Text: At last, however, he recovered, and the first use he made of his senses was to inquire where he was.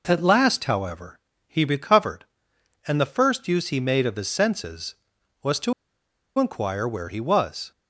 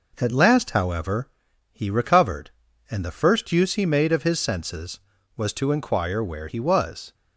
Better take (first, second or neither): second